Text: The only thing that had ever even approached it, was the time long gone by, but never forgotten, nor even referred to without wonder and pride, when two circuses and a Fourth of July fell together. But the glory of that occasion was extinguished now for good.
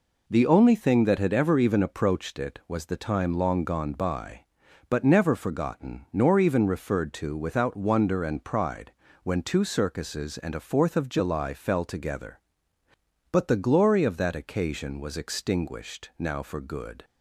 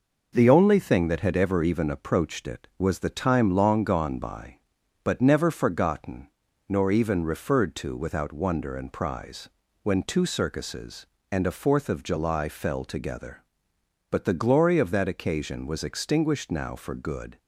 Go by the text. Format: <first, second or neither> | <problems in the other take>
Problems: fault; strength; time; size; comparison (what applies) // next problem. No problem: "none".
first | says "prize" for "pride"; at 8.9 s